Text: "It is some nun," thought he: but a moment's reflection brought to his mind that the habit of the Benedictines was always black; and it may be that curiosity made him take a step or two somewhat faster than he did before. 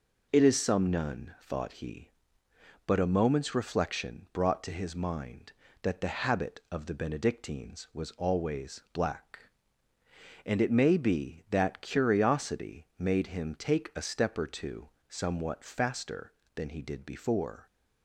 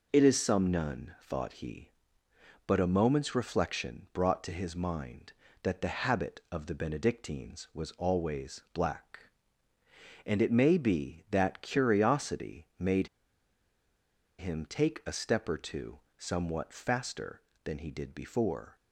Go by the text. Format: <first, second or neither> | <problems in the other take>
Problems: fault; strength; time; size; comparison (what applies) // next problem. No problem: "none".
first | pauses between "made" and "him"; strong; at 13.0 s; 1.3 s long // pauses between "two" and "somewhat"; slight; at 15.9 s; 0.18 s long; slight in the first